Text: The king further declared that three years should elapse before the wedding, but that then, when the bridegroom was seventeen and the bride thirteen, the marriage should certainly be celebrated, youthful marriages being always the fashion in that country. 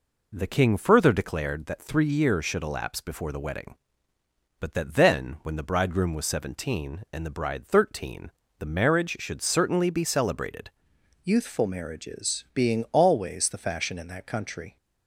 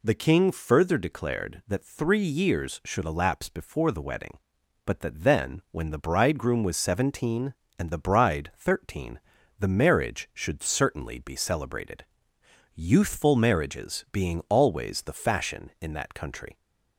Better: second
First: changes voice at "youthful"; from 11.2 s on; 3.5 s long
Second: none

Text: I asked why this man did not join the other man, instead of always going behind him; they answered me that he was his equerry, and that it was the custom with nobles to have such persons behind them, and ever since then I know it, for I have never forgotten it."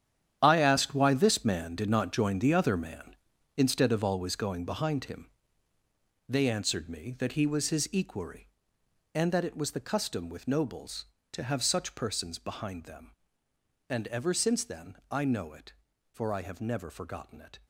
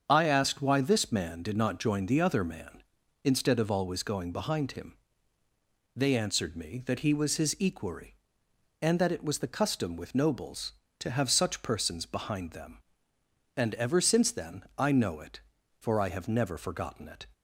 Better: second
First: gets quieter; strong; throughout; 12.5 dB // starts louder than the rest; strong; until 1.4 s; 10 dB // pauses between "then" and "I"; slight; at 14.9 s; 0.16 s long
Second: starts louder than the rest; strong; until 1.0 s; 7.5 dB // pauses between "then" and "I"; slight; at 14.6 s; 0.16 s long

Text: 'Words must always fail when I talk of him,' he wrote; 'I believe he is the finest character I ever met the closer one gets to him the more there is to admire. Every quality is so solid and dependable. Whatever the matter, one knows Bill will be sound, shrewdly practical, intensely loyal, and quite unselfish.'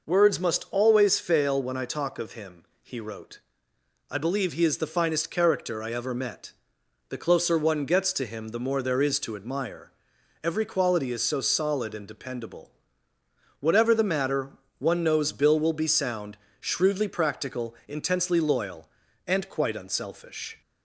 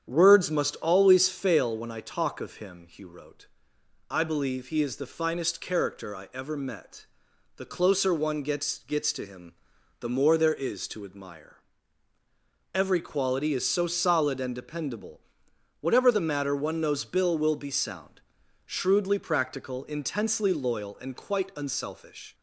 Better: first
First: pauses between "met" and "the"; noticeable; at 6.5 s; 0.58 s long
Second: starts louder than the rest; strong; until 1.1 s; 8.5 dB // pauses between "met" and "the"; noticeable; at 7.0 s; 0.52 s long // says "gets" twice; at 8.7 s // pauses between "him" and "the"; noticeable; at 9.5 s; 0.48 s long

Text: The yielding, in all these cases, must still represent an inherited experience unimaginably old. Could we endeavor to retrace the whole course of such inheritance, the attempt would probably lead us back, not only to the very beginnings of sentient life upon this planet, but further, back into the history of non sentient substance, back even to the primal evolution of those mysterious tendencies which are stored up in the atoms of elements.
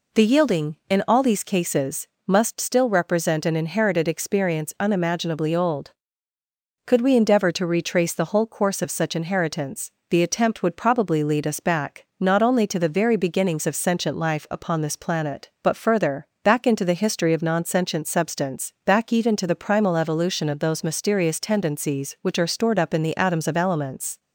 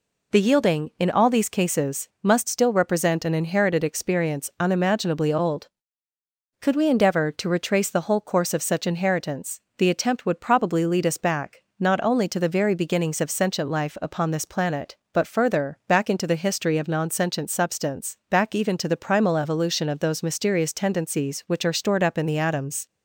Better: first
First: none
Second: stops before "of elements"; at 22.8 s

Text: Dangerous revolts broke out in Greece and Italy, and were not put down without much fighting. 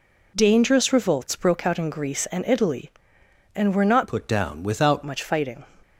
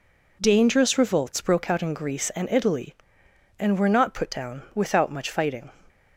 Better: second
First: changes voice from "put" to "without"; from 4.0 to 5.0 s; 1.0 s long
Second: none

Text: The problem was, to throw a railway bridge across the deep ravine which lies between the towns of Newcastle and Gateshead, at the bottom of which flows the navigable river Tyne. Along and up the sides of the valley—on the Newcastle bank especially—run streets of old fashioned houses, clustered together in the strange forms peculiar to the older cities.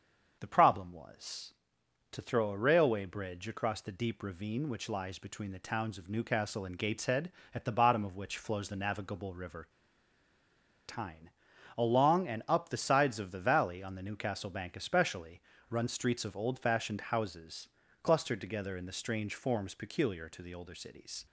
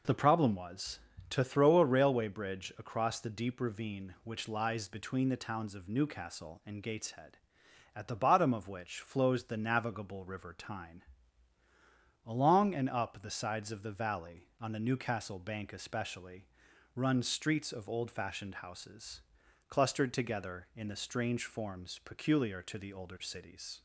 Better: second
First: starts louder than the rest; until 1.4 s; 7 dB // pauses between "river" and "Tyne"; at 9.6 s; 1.1 s long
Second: none

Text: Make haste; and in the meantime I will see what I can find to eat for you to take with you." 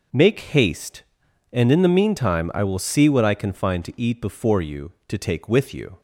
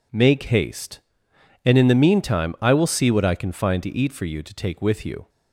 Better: second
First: says "before" for "for"; at 4.2 s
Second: none

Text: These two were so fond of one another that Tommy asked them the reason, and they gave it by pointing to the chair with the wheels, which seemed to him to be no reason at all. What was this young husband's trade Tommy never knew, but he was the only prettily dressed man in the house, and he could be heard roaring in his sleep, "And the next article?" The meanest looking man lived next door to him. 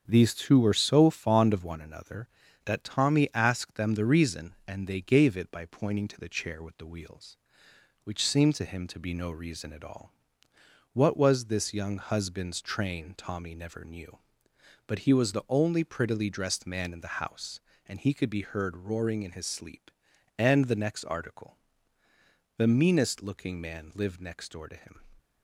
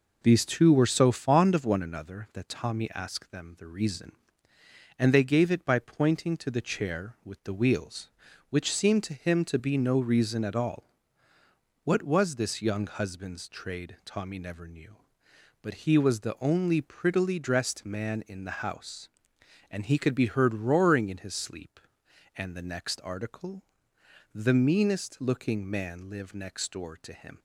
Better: second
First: starts louder than the rest; strong; until 1.0 s; 7 dB // says "train" for "trade"; at 12.6 s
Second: none

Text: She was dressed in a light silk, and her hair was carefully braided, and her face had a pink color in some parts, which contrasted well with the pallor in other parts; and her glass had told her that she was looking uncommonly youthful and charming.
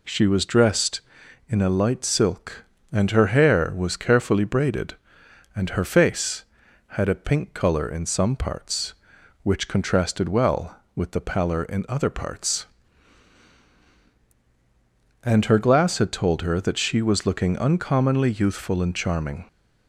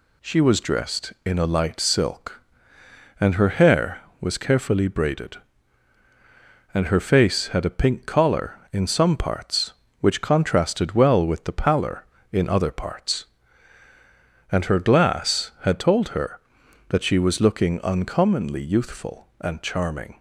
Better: first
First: none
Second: says "collar" for "color"; at 8.0 s

